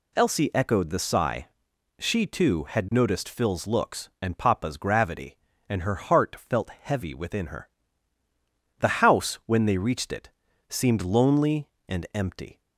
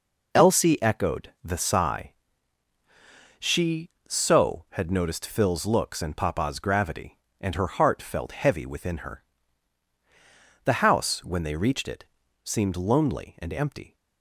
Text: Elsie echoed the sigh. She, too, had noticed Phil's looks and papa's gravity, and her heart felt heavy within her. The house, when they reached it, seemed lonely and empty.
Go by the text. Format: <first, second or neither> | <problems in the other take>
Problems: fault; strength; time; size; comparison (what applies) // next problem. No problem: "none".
first | says "so" for "too"; at 4.0 s